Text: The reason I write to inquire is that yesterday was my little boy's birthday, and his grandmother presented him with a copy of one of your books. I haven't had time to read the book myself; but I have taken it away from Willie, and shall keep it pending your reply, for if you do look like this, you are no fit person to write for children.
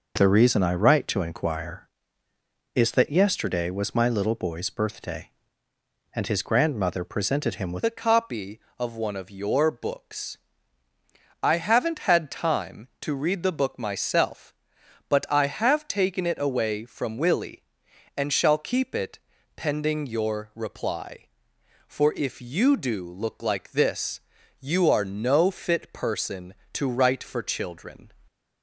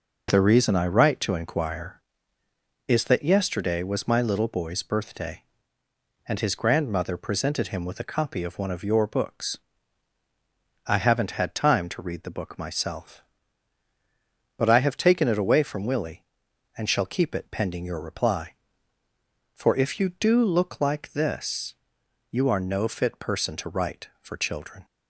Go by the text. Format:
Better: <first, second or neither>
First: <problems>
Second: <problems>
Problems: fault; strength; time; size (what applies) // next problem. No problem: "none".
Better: second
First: changes voice at "a"; from 7.8 s on; 20.3 s long // pauses between "it" and "pending"; at 19.1 s; 0.38 s long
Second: none